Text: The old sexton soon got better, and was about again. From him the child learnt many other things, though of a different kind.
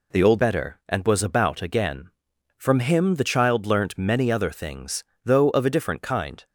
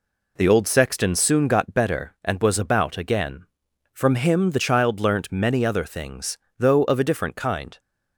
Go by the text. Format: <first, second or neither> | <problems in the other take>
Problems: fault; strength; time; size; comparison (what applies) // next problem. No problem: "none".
second | skips "sexton soon got"; at 0.3 s